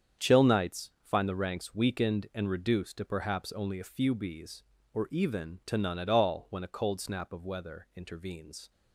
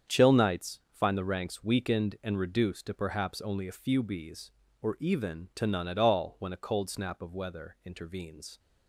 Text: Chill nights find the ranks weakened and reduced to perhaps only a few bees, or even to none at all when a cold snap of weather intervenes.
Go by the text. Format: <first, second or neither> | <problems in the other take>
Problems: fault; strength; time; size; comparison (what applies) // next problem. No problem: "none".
neither | starts louder than the rest; strong; the same in both